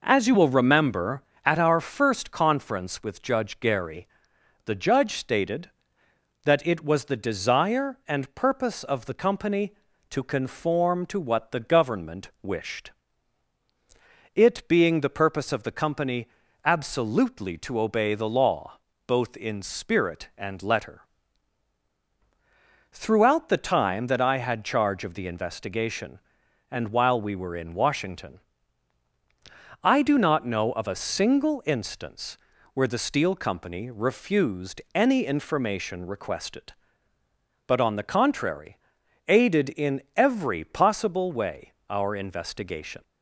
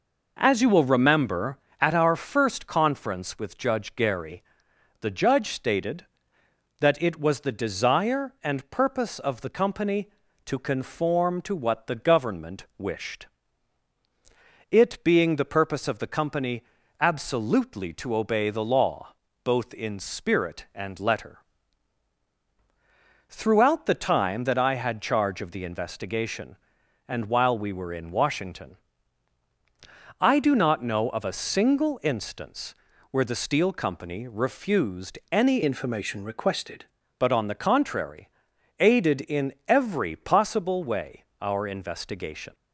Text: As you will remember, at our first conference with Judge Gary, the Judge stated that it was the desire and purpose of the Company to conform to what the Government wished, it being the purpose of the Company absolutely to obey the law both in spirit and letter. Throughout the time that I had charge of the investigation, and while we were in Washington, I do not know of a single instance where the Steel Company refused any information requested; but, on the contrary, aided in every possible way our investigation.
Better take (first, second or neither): first